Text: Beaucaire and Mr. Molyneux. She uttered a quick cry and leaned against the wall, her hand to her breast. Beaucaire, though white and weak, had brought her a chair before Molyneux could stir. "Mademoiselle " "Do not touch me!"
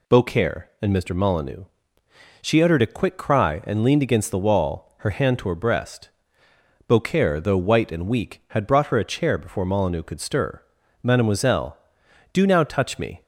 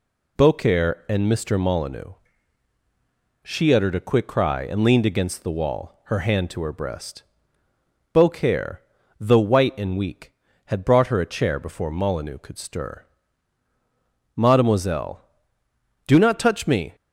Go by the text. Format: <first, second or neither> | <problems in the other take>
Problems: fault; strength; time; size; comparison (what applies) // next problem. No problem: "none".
second | says "now" for "not"; at 12.4 s